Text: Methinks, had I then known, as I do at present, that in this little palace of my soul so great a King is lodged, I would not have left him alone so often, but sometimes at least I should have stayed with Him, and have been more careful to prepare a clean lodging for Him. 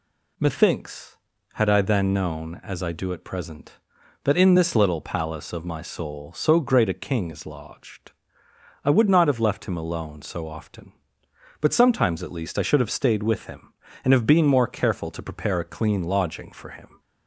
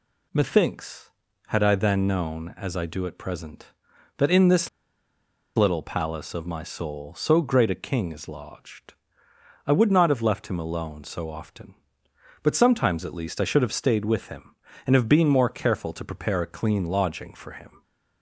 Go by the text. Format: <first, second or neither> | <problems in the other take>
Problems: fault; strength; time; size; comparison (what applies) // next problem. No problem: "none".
first | pauses between "this" and "little"; noticeable; at 4.6 s; 0.87 s long